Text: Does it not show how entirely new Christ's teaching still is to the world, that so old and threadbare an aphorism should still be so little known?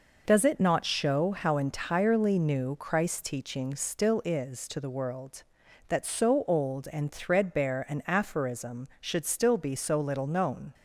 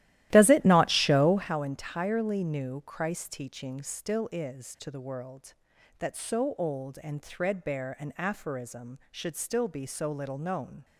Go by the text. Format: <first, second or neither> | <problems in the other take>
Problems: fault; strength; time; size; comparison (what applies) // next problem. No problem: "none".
first | starts louder than the rest; strong; until 1.5 s; 14.5 dB